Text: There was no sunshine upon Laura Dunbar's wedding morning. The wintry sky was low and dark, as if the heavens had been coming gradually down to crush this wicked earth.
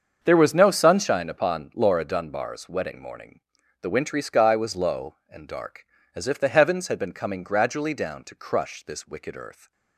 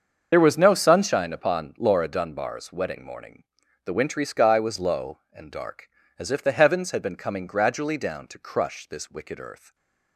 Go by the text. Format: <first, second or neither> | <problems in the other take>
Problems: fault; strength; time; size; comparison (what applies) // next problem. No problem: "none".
first | loses the start of "There"; at 0.3 s; 55 ms // starts louder than the rest; until 1.3 s; 6.5 dB; also in the first